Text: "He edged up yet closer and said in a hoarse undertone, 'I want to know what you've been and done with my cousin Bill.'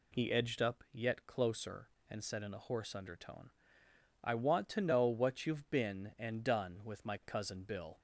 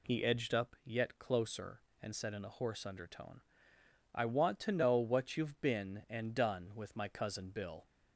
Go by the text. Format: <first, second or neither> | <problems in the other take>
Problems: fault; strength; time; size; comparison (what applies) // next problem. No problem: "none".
neither | none